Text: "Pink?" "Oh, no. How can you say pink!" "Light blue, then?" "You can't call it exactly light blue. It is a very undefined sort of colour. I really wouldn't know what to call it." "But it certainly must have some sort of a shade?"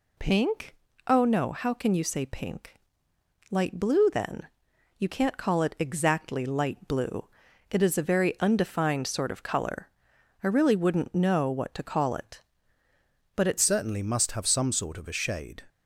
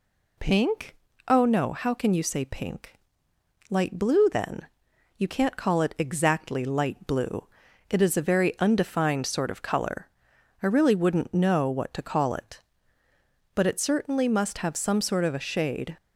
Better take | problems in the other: second | changes voice at "certainly"; from 13.5 s on; 2.1 s long

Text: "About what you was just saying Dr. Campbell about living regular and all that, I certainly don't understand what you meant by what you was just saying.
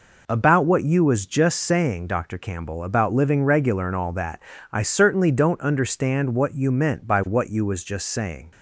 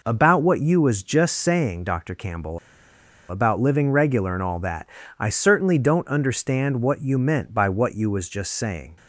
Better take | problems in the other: first | pauses between "Campbell" and "about"; noticeable; at 2.5 s; 0.71 s long

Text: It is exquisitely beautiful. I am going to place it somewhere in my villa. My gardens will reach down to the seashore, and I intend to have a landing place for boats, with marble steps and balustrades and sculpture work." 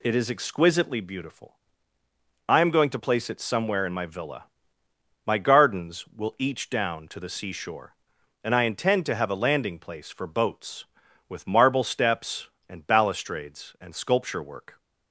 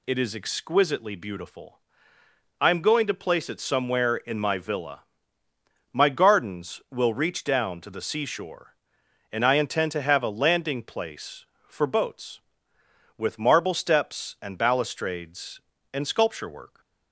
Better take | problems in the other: second | says "each" for "reach"; at 6.3 s

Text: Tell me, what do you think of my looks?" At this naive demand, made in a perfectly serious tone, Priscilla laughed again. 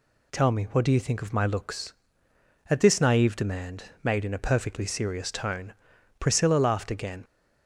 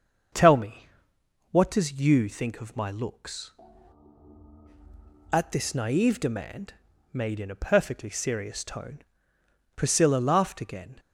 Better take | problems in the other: first | starts louder than the rest; until 1.9 s; 6.5 dB // says "does" for "do"; at 1.6 s

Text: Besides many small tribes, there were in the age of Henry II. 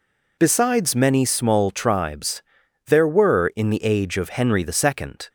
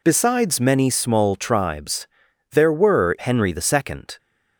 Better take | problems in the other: first | skips "in the age of"; at 3.1 s

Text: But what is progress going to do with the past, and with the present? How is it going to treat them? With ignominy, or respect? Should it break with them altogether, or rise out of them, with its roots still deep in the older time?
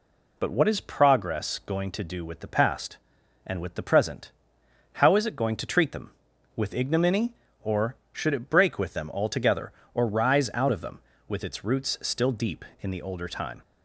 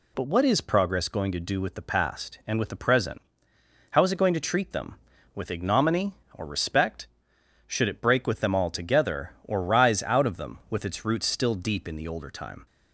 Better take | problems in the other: second | skips "respect"; at 8.0 s

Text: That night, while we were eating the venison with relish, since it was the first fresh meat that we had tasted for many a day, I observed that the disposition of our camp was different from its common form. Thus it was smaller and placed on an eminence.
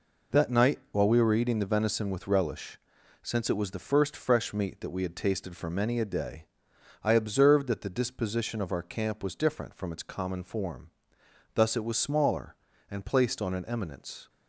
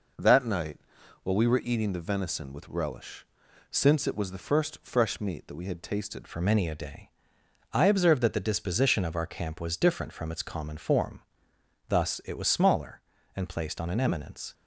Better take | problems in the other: first | changes voice at "for"; from 6.2 s on; 8.3 s long

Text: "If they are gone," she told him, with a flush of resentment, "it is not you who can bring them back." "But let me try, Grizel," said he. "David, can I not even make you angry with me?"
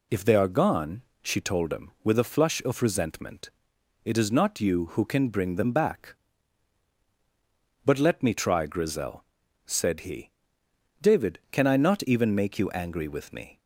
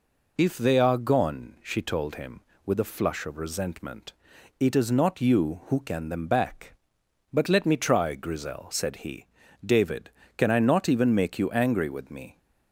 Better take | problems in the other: first | skips "bring"; at 6.0 s

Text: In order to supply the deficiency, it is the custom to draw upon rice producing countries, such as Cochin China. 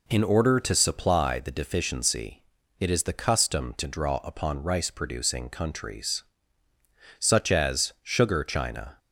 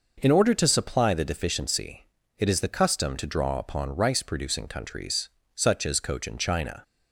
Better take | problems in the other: second | says "Sugar" for "Cochin"; at 8.0 s

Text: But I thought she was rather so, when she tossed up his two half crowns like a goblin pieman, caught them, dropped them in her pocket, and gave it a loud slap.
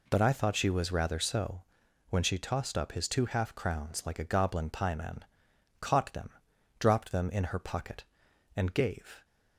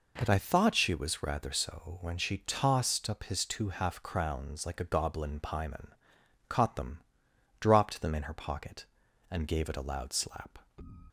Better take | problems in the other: second | stops before "it a loud slap"; at 9.2 s

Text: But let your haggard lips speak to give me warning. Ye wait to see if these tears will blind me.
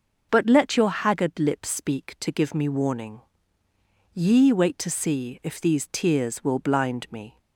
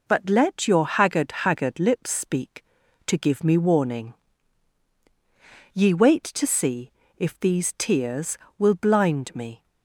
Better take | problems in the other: first | says "haggard" twice; at 1.4 s // pauses between "see" and "if"; slight; at 6.9 s; 0.26 s long

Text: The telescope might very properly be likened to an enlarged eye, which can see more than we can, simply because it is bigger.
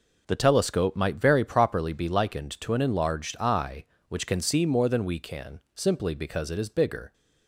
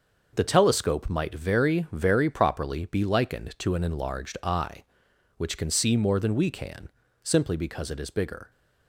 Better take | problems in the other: first | starts louder than the rest; noticeable; until 1.3 s; 6 dB // says "very" twice; at 1.9 s

